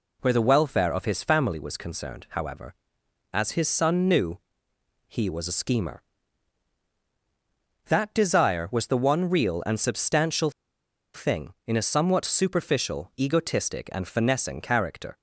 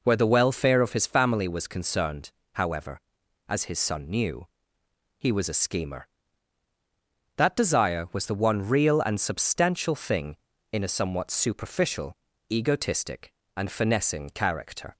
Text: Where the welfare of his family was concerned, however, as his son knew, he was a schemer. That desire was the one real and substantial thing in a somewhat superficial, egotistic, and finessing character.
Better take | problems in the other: second | pauses between "substantial" and "thing"; noticeable; at 10.4 s; 0.64 s long

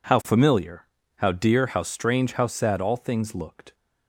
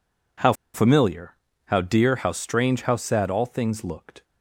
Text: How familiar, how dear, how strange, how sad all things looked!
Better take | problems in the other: first | pauses between "How" and "familiar"; slight; at 0.5 s; 0.21 s long

